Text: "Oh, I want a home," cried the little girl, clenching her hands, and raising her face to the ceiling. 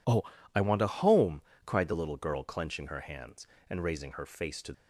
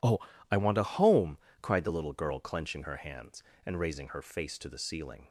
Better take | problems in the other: second | stops before "the ceiling"; at 4.7 s

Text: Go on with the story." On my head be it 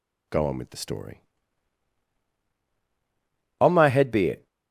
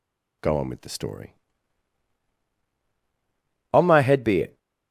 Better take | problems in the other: neither | none

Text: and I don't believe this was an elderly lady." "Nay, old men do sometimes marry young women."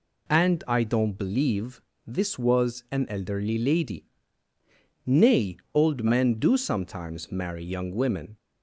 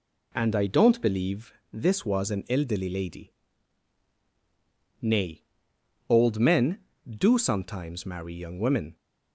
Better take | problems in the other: neither | pauses between "believe" and "this"; slight; the same in both

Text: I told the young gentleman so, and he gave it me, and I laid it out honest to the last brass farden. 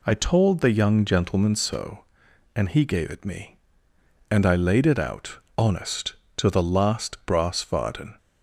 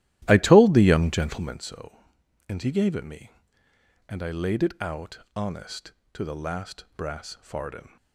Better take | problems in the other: first | starts louder than the rest; strong; until 1.6 s; 14 dB // pauses between "out" and "honest"; slight; at 5.1 s; 0.18 s long; slight in the first

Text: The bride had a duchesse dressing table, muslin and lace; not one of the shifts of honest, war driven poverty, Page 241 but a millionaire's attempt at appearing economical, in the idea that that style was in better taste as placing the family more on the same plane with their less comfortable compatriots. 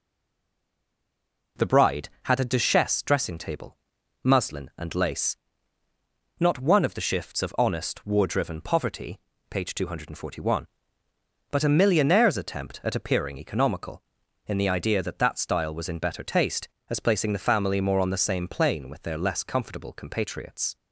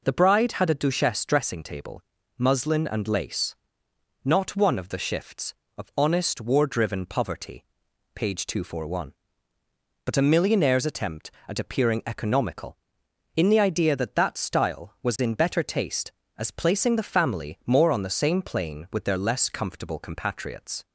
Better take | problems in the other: second | stays silent before the first word; noticeable; until 1.5 s; 1.5 s long

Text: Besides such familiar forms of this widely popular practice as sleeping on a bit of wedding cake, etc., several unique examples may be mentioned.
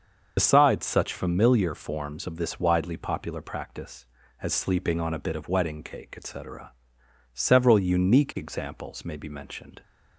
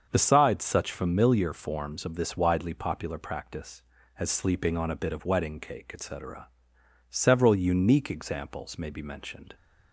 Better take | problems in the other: second | loses the start of "Besides"; at 0.3 s; 65 ms // starts louder than the rest; until 1.3 s; 6.5 dB; also in the second

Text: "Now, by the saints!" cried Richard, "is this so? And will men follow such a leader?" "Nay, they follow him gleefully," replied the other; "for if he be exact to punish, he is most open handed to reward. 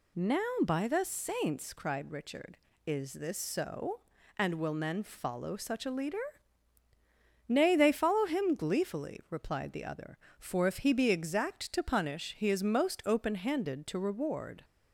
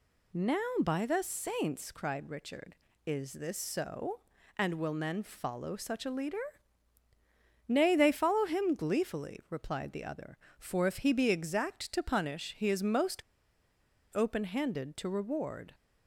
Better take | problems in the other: first | pauses between "most" and "open"; noticeable; at 13.2 s; 0.91 s long

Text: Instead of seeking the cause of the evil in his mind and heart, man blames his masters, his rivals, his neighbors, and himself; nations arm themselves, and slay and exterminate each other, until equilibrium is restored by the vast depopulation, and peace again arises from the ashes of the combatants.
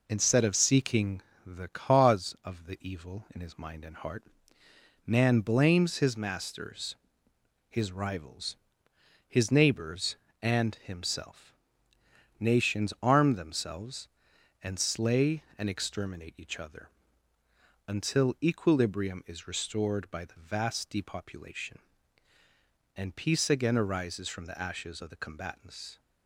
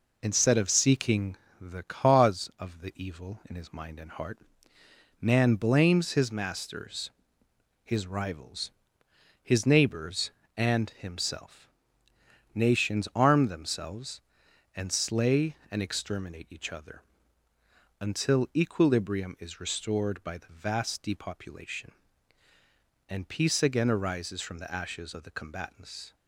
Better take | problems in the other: neither | pauses between "seeking" and "the"; slight; the same in both

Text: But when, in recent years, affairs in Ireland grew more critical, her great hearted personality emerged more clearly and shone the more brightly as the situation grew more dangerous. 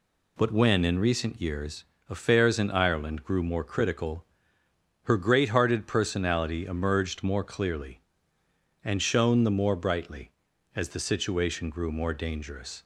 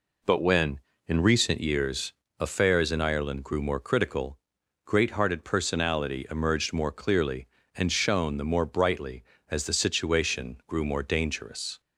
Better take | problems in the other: first | skips "her"; at 4.6 s

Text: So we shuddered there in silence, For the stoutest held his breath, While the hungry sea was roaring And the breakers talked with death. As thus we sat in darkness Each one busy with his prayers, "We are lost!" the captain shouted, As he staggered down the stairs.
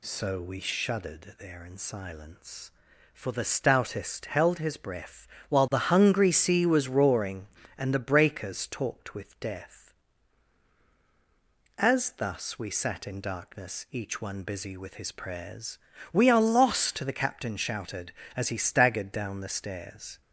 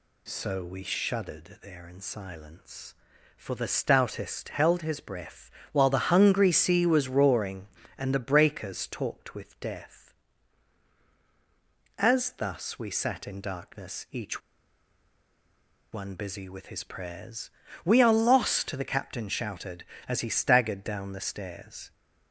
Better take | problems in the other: first | pauses between "Each" and "one"; strong; at 14.4 s; 1.5 s long

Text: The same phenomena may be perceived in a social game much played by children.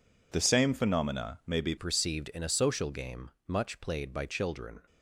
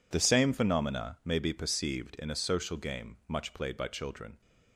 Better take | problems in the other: second | changes voice at "perceived"; from 1.7 s on; 3.0 s long // pauses between "game" and "much"; slight; at 3.3 s; 0.16 s long

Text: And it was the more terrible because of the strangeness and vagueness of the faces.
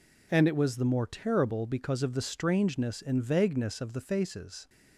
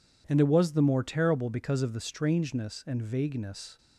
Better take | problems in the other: first | stops before "of the faces"; at 3.7 s

